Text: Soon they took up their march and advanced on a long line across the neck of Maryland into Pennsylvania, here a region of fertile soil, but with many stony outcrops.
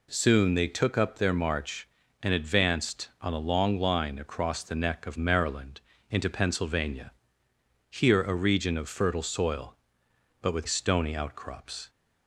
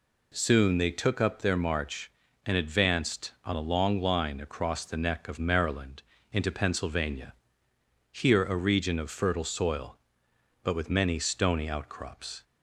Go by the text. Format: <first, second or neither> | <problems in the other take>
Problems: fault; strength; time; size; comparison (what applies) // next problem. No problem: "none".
second | pauses between "Maryland" and "into"; slight; at 5.7 s; 0.30 s long; slight in the second // skips "many"; at 10.6 s